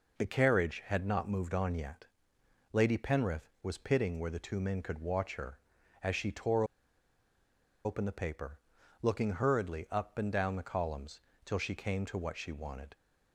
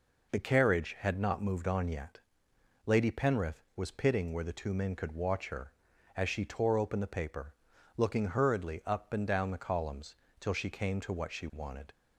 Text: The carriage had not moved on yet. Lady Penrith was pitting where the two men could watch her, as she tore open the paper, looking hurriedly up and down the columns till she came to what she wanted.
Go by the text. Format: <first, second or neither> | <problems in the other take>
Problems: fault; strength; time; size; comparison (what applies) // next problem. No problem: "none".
second | pauses between "tore" and "open"; at 6.6 s; 1.2 s long // pauses between "columns" and "till"; slight; at 11.2 s; 0.24 s long; slight in the second